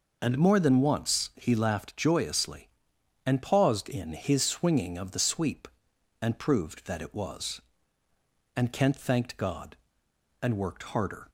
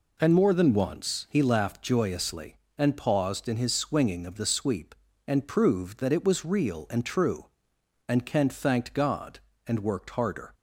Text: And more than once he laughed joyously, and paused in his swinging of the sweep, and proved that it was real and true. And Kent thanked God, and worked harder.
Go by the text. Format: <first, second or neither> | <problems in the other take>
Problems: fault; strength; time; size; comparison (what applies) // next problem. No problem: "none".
second | skips "real and true"; at 8.0 s